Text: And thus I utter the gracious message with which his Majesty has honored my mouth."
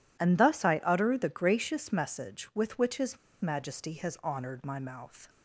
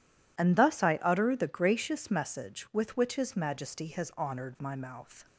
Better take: second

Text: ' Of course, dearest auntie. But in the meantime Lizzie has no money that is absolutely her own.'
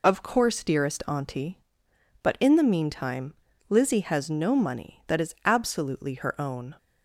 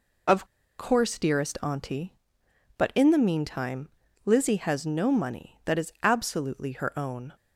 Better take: first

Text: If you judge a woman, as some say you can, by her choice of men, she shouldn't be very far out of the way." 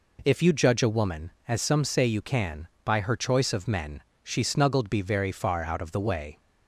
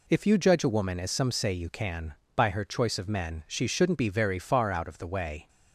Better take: second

